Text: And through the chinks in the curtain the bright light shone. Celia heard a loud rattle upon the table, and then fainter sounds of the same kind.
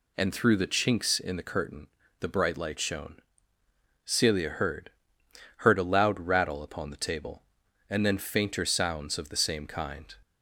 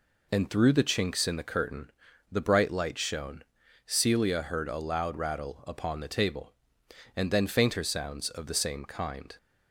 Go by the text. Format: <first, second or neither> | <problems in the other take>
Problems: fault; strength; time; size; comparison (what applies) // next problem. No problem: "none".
second | pauses between "curtain" and "the"; slight; at 1.8 s; 0.32 s long; also in the second // says "heard" twice; at 5.5 s